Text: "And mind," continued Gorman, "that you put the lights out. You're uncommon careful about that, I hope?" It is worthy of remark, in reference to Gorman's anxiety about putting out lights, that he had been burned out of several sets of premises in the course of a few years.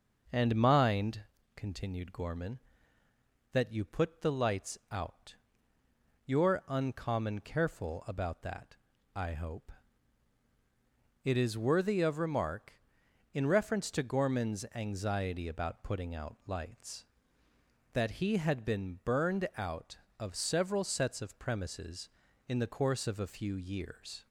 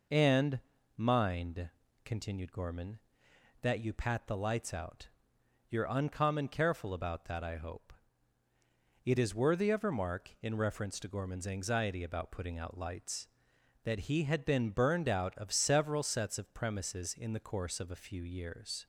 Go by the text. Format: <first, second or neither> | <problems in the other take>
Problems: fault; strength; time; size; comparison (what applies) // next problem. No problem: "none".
first | pauses between "And" and "mind"; slight; at 0.6 s; 0.36 s long // says "pat" for "put"; at 3.9 s